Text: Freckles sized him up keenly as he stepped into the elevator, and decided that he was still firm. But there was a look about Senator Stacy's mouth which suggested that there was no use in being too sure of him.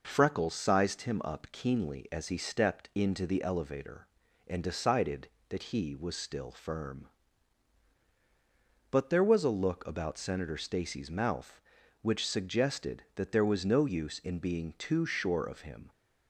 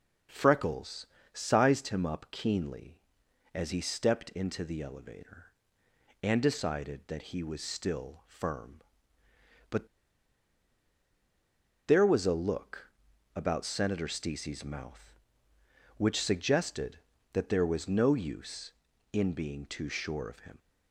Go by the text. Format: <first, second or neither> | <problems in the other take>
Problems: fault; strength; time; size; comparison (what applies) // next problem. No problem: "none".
first | pauses between "Freckles" and "sized"; slight; at 1.0 s; 0.26 s long // pauses between "But" and "there"; strong; at 9.8 s; 2.0 s long // pauses between "look" and "about"; at 12.9 s; 0.44 s long